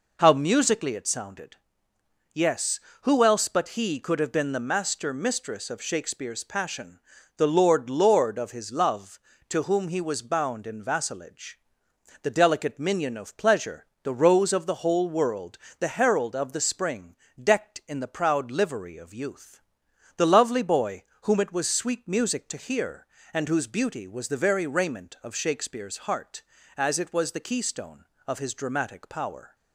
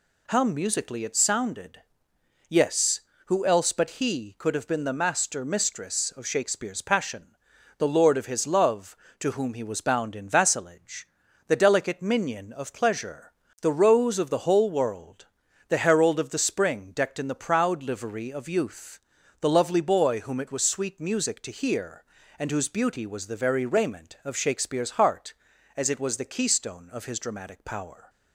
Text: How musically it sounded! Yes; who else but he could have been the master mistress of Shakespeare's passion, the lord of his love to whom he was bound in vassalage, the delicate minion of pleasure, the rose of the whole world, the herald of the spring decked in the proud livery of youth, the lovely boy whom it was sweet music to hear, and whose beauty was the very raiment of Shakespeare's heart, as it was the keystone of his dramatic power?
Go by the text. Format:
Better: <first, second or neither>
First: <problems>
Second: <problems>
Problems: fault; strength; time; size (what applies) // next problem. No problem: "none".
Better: second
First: says "lord" twice; at 7.8 s // pauses between "spring" and "decked"; slight; at 17.1 s; 0.24 s long // pauses between "boy" and "whom"; slight; at 21.0 s; 0.20 s long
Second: none